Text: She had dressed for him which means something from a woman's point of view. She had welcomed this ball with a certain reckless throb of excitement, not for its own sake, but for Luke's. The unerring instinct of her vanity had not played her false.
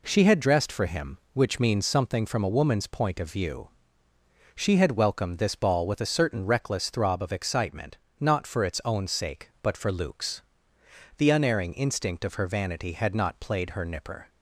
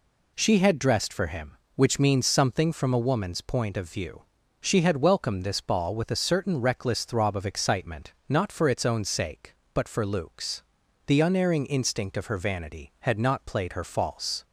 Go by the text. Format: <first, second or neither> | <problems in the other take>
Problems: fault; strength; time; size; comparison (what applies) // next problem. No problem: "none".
second | says "nipper" for "false"; at 13.8 s